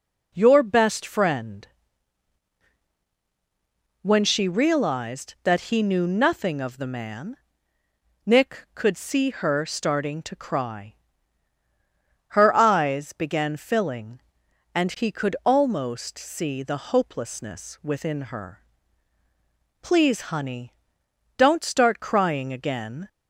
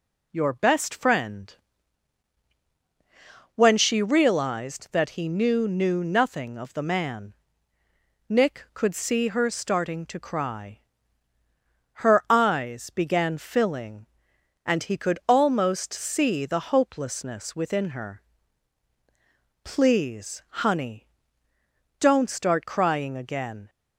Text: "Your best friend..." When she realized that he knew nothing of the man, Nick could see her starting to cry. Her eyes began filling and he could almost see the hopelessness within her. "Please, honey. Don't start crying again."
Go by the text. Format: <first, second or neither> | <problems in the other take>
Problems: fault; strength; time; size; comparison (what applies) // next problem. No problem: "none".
first | says "knew" twice; at 5.6 s